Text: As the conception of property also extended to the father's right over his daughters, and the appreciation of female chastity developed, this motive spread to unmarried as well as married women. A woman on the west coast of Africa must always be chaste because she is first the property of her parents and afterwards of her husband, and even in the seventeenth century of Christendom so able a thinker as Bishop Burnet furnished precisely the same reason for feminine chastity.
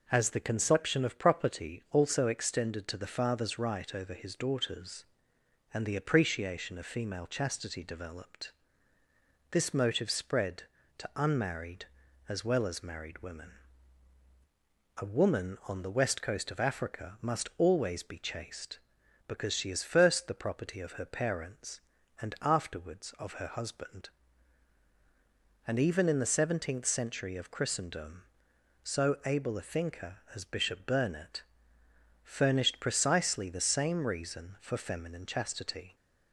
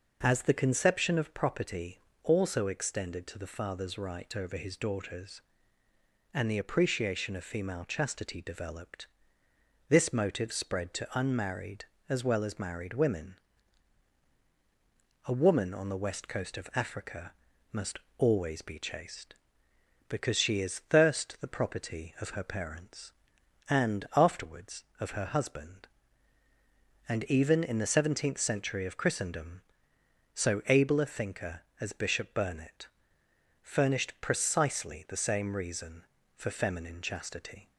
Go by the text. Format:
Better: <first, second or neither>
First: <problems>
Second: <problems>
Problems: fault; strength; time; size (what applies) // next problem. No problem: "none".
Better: first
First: pauses between "Burnet" and "furnished"; noticeable; at 31.4 s; 0.82 s long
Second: pauses between "property" and "also"; slight; at 1.9 s; 0.22 s long // pauses between "Africa" and "must"; at 17.3 s; 0.40 s long // pauses between "must" and "always"; slight; at 17.9 s; 0.20 s long // says "thirst" for "first"; at 20.8 s // pauses between "Burnet" and "furnished"; noticeable; at 32.8 s; 0.74 s long